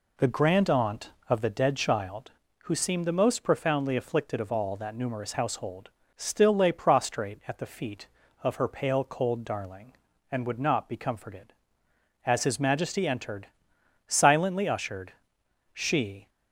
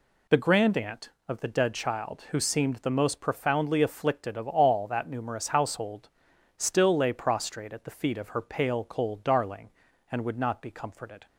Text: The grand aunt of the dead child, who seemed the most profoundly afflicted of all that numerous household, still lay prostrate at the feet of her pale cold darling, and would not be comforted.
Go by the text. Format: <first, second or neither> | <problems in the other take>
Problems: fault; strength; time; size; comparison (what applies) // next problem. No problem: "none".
second | goes on to say "As his Majesty entered silently ushered she"; strong; from 12.2 s on; 4.0 s long